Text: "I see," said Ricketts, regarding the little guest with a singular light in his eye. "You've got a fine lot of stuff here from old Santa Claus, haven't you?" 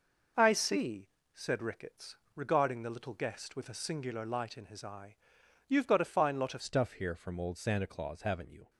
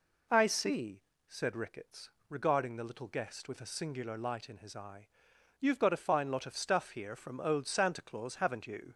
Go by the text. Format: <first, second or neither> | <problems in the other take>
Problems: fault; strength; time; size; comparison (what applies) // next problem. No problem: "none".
second | changes voice at "stuff"; from 6.6 s on; 2.0 s long